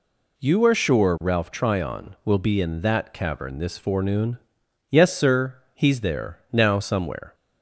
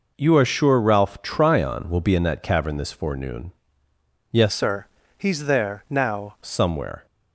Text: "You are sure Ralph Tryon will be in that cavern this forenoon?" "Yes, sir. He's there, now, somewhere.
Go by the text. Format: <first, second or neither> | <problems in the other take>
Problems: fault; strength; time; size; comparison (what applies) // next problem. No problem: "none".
first | changes voice from "sir" to "now"; from 4.5 to 6.3 s; 1.8 s long